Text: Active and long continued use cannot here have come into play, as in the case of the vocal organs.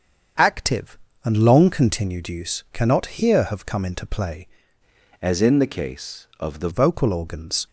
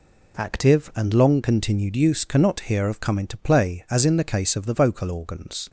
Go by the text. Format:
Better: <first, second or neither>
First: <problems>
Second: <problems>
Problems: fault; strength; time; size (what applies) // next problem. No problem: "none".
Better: second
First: starts louder than the rest; strong; until 1.6 s; 7 dB // changes voice from "as" to "the"; from 5.2 to 6.6 s; 1.4 s long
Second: none